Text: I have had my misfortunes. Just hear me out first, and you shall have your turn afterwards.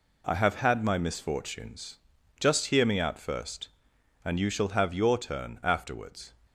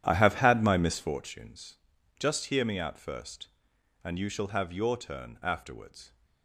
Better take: first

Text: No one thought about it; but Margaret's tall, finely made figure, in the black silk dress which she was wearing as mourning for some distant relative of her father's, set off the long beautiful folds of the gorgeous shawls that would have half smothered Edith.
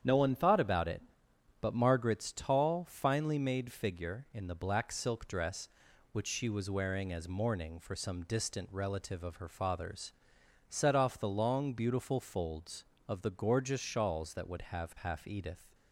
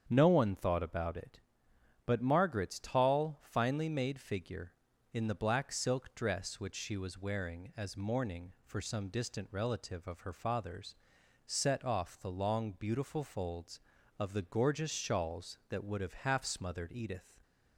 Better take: second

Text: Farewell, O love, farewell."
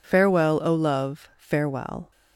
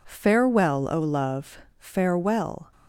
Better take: neither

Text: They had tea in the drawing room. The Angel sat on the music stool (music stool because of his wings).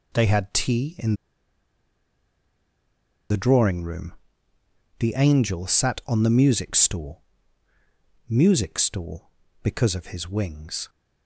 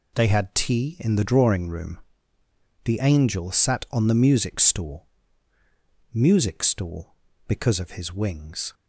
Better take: second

